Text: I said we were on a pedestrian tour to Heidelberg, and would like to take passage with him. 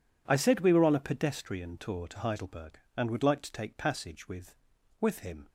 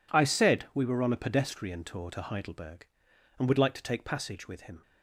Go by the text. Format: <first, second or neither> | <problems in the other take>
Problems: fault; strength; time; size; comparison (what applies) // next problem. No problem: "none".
second | says "with" twice; at 5.0 s